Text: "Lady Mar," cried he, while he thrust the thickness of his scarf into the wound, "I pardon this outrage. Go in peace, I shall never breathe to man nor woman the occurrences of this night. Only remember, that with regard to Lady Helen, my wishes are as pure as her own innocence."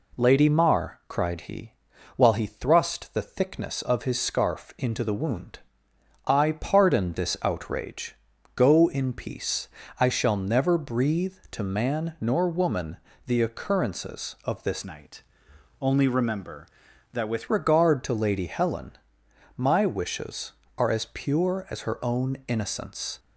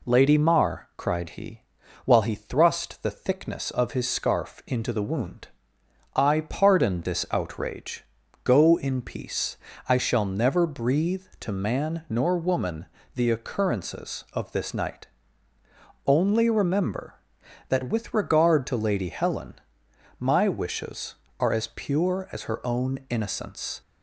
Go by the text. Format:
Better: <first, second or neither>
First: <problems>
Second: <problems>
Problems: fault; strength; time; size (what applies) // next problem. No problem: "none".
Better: second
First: pauses between "woman" and "the"; slight; at 12.9 s; 0.28 s long // changes voice from "night" to "with"; from 14.8 to 17.4 s; 2.6 s long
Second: pauses between "woman" and "the"; slight; at 12.8 s; 0.28 s long